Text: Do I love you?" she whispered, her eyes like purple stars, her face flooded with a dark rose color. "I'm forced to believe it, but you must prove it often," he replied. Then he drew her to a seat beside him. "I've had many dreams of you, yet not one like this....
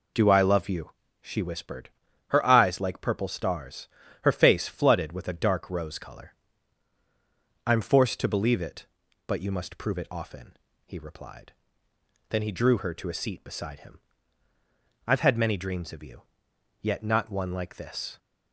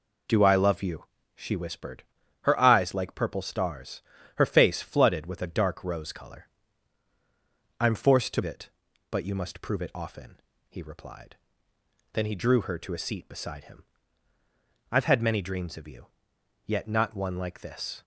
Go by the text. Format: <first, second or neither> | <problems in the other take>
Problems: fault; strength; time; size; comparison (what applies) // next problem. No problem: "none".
first | skips "believe"; at 8.4 s